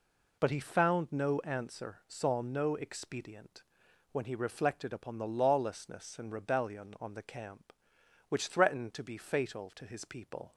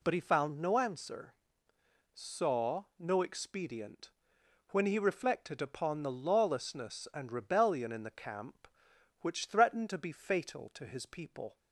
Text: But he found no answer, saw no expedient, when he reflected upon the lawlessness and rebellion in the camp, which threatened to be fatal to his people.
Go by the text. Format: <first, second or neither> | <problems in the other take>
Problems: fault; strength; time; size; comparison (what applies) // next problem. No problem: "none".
second | says "on" for "in"; at 6.9 s